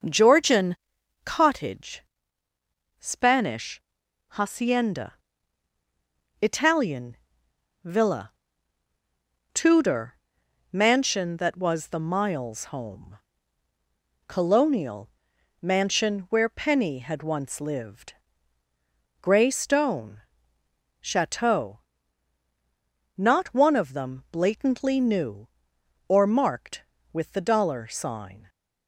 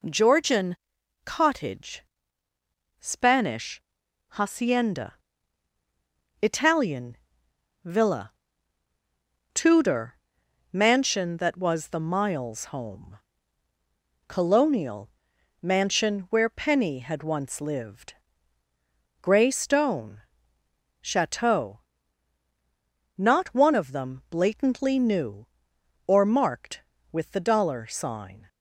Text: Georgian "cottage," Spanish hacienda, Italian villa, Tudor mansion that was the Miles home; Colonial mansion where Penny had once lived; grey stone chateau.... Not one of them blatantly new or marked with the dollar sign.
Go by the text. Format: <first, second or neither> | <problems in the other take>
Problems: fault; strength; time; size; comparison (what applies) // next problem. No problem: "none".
second | starts louder than the rest; noticeable; until 1.7 s; 6 dB // pauses between "Georgian" and "cottage"; noticeable; at 0.7 s; 0.50 s long; noticeable in the second // pauses between "Spanish" and "hacienda"; noticeable; at 3.7 s; 0.50 s long; noticeable in the second // pauses between "Italian" and "villa"; noticeable; at 7.1 s; 0.66 s long; noticeable in the second // pauses between "Tudor" and "mansion"; noticeable; at 10.1 s; 0.56 s long; noticeable in the second // pauses between "Colonial" and "mansion"; noticeable; at 15.0 s; 0.54 s long; noticeable in the second // pauses between "stone" and "chateau"; noticeable; at 20.2 s; 0.78 s long; noticeable in the second